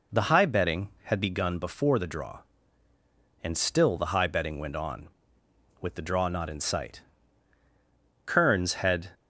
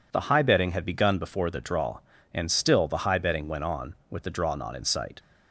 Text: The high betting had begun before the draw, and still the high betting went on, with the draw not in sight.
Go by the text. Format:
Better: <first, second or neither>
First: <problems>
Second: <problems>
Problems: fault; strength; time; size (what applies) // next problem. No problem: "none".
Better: second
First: goes on to say "Kearns had"; noticeable; from 8.2 s on; 0.86 s long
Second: none